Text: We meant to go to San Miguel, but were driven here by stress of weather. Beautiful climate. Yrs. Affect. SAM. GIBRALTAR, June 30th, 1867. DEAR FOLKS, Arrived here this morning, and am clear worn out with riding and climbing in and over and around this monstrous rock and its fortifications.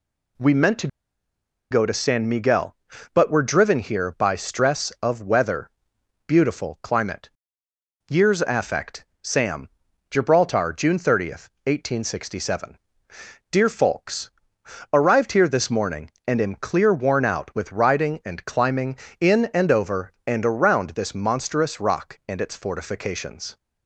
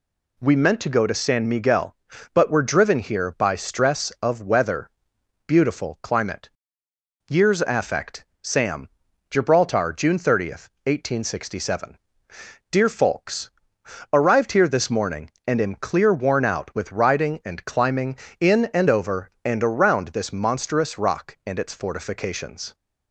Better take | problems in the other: second | pauses between "to" and "go"; noticeable; at 0.8 s; 0.83 s long

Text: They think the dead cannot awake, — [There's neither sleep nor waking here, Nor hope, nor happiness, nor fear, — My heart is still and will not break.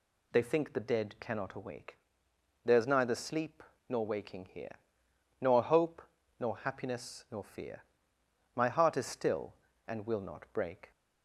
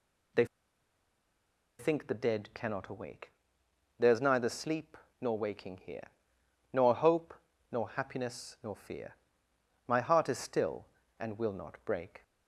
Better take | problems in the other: first | pauses between "They" and "think"; strong; at 0.4 s; 1.3 s long // pauses between "sleep" and "nor"; slight; at 4.9 s; 0.24 s long; slight in the first

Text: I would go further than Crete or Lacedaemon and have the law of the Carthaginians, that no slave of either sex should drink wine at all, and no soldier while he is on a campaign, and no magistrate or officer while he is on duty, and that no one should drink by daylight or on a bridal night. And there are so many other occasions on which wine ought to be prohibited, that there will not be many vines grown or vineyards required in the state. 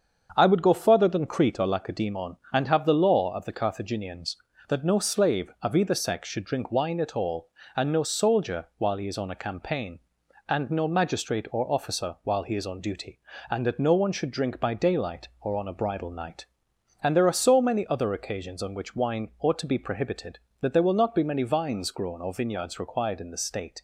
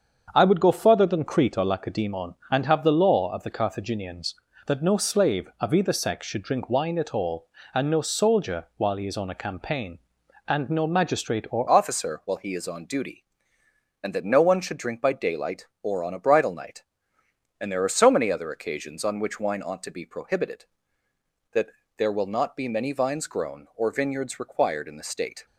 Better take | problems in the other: first | starts louder than the rest; until 1.3 s; 7 dB; also in the first // changes voice at "officer"; from 11.6 s on; 13.8 s long // pauses between "that" and "there"; slight; at 21.6 s; 0.28 s long

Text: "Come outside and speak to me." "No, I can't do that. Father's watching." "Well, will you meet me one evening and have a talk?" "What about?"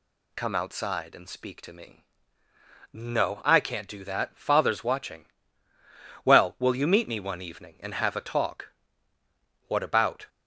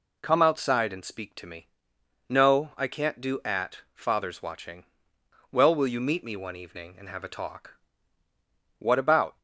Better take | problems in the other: first | says "at" for "that"; at 3.4 s

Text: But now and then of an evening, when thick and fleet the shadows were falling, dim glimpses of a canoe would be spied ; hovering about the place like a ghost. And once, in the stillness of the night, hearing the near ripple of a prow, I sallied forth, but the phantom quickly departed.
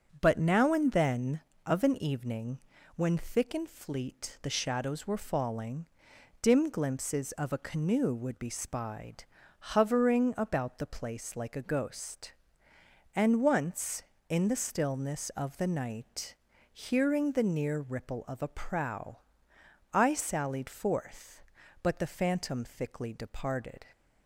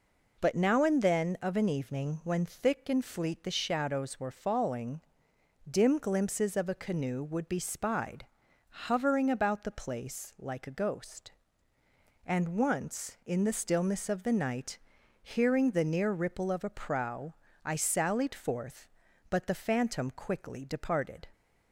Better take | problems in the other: second | starts louder than the rest; until 1.1 s; 6.5 dB // says "thickly" for "quickly"; at 22.6 s

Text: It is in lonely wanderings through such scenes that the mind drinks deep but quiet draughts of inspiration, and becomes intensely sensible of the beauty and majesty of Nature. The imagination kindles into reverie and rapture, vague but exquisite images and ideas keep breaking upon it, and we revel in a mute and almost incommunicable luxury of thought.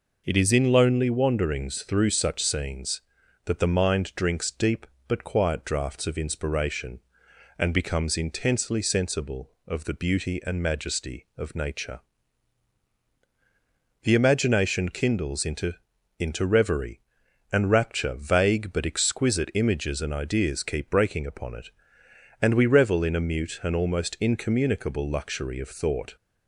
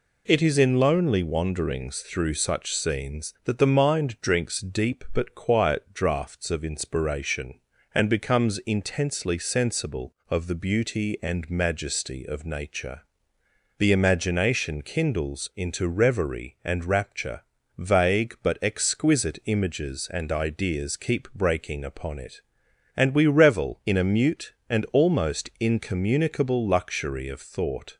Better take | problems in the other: second | says "into" twice; at 16.1 s

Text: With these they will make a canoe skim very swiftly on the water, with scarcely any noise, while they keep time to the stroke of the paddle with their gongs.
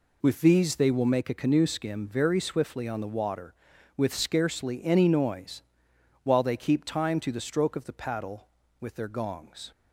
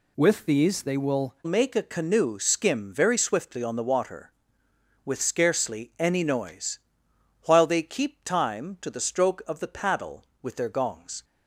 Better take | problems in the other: first | changes voice at "make"; from 1.4 s on; 9.8 s long

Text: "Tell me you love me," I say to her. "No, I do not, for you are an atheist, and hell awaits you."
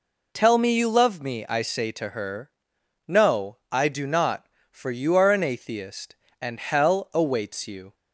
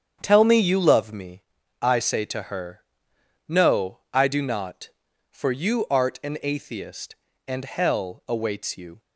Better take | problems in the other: first | starts louder than the rest; strong; until 1.2 s; 8 dB // says "art" for "are"; at 5.8 s

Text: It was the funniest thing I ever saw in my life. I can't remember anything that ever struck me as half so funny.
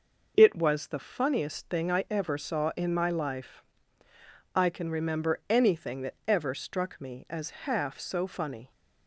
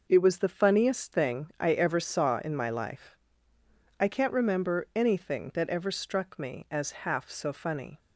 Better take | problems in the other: second | says "can" for "can't"; at 4.6 s

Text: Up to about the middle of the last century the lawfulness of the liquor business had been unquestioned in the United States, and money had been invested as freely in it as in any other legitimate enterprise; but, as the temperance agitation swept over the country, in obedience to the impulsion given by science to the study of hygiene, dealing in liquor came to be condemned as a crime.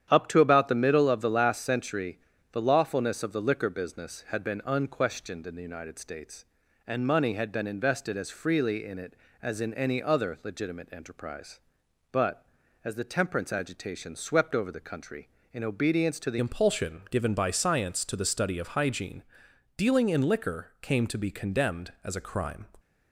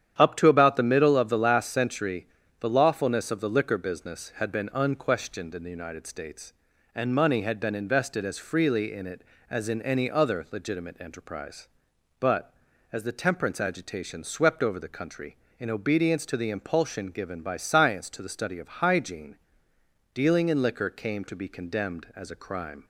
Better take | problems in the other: second | starts louder than the rest; strong; until 1.1 s; 9.5 dB; strong in the second // pauses between "century" and "the"; slight; at 2.1 s; 0.34 s long; slight in the second // changes voice at "impulsion"; from 16.3 s on; 6.3 s long

